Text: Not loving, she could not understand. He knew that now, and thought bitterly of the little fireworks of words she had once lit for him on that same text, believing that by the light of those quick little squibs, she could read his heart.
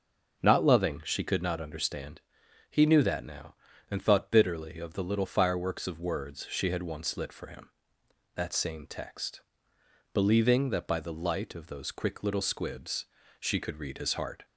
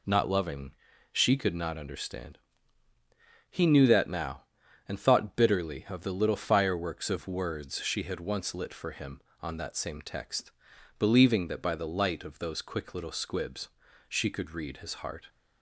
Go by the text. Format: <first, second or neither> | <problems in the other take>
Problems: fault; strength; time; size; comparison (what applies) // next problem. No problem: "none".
second | skips "on"; at 8.0 s